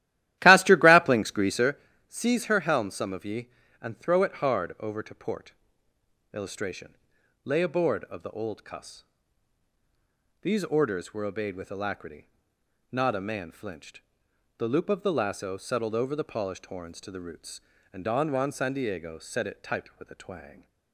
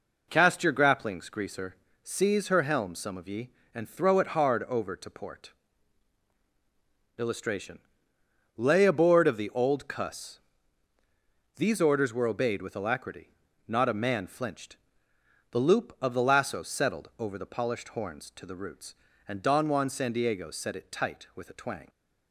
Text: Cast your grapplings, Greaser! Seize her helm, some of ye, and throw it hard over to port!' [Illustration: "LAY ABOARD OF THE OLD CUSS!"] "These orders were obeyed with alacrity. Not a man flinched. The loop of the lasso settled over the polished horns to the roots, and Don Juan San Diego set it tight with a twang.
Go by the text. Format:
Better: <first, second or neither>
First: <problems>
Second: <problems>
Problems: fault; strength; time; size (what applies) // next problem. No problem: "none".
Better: second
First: starts louder than the rest; strong; until 1.7 s; 14.5 dB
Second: none